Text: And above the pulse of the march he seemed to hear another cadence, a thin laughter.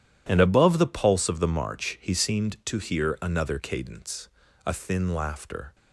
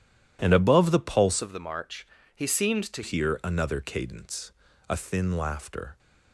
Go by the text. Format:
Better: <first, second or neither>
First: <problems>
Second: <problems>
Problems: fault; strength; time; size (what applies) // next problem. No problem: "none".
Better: first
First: none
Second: changes voice from "of" to "to"; from 1.4 to 3.0 s; 1.6 s long // pauses between "march" and "he"; slight; at 2.0 s; 0.28 s long